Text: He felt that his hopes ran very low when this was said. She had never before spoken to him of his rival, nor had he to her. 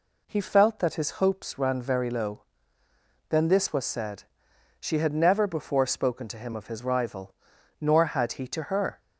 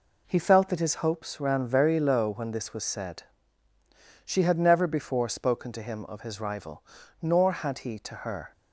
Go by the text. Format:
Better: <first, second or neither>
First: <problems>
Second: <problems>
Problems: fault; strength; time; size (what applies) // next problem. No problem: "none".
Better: second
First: says "then" for "when"; at 3.2 s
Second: none